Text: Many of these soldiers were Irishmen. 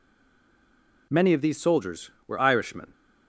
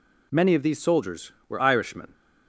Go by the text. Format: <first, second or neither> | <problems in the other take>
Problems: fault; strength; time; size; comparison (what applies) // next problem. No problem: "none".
second | stays silent before the first word; until 1.1 s; 1.1 s long